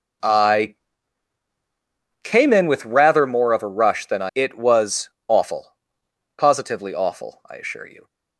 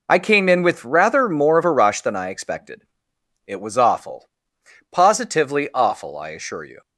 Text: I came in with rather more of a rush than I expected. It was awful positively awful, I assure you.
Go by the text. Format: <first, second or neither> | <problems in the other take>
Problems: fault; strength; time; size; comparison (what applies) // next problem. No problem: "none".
second | pauses between "I" and "came"; strong; at 0.7 s; 1.4 s long // skips "expected"; at 4.3 s // pauses between "was" and "awful"; slight; at 5.0 s; 0.18 s long // pauses between "awful" and "positively"; noticeable; at 5.7 s; 0.64 s long; noticeable in the second